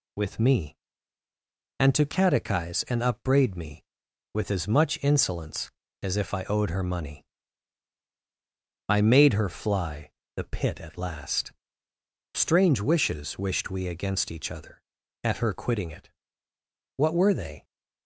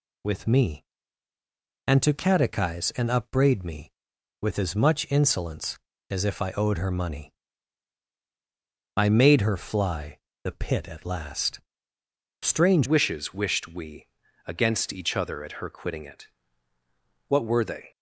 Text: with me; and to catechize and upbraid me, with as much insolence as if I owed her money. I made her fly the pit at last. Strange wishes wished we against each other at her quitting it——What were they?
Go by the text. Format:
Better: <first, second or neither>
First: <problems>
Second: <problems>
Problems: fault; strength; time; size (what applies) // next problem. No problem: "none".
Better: first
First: pauses between "fly" and "the"; slight; at 10.1 s; 0.26 s long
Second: pauses between "fly" and "the"; slight; at 10.1 s; 0.26 s long // changes voice at "wishes"; from 12.8 s on; 5.1 s long // pauses between "we" and "against"; at 14.0 s; 0.40 s long